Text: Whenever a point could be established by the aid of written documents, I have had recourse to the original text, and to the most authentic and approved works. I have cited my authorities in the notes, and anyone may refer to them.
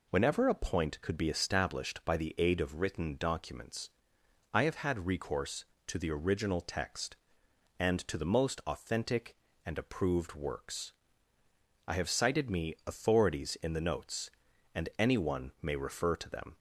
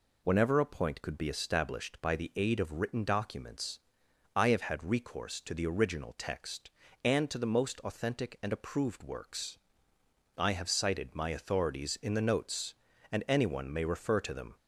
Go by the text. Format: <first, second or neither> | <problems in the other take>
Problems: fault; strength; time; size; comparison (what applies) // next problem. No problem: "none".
second | says "me" for "my"; at 12.4 s